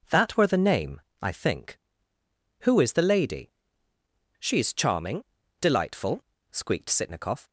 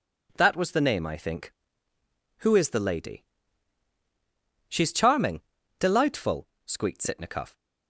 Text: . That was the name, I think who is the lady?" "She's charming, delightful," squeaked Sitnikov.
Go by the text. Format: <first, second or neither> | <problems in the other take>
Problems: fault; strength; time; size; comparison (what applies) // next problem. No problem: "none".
second | says "were" for "was"; at 0.3 s